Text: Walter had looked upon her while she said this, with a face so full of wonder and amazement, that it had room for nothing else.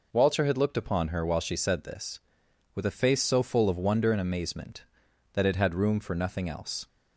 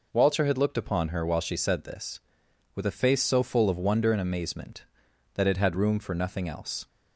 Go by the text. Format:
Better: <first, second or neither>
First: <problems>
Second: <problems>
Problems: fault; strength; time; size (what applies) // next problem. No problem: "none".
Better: neither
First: none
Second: none